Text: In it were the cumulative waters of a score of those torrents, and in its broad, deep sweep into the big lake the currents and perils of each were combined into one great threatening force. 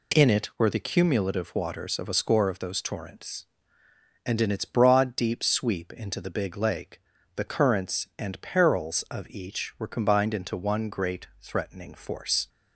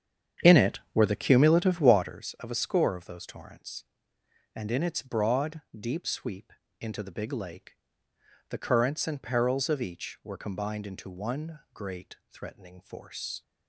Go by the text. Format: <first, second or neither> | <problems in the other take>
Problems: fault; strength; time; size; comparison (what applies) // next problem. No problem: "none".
first | starts louder than the rest; strong; until 2.1 s; 8.5 dB // pauses between "sweep" and "into"; slight; at 6.5 s; 0.28 s long // pauses between "lake" and "the"; noticeable; at 7.7 s; 0.76 s long; slight in the first